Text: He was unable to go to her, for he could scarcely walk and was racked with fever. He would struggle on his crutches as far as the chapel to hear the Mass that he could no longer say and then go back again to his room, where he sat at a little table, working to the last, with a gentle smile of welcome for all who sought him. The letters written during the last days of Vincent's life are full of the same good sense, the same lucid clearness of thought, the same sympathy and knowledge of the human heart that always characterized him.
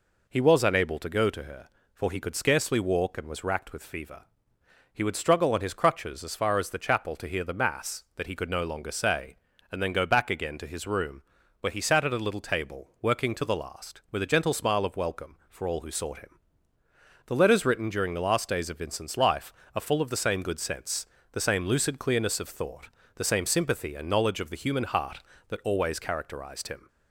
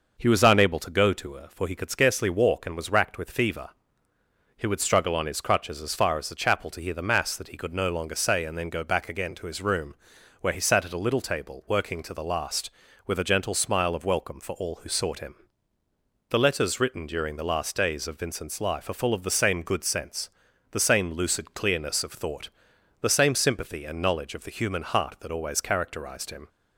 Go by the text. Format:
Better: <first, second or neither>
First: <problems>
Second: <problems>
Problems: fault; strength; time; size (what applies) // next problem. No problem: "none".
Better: neither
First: none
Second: none